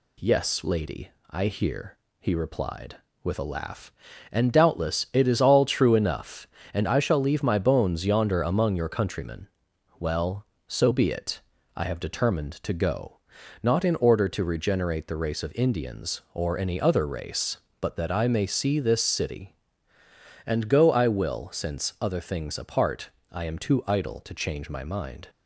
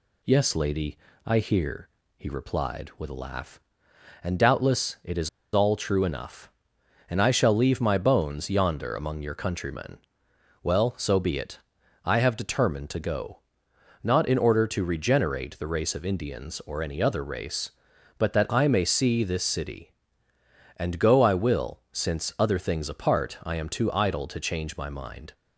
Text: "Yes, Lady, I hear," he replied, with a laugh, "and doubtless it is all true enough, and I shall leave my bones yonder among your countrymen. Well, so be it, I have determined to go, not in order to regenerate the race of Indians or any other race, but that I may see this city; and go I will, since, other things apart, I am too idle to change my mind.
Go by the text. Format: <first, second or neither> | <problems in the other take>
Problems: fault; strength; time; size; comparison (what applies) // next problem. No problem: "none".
first | pauses between "is" and "all"; slight; at 5.2 s; 0.26 s long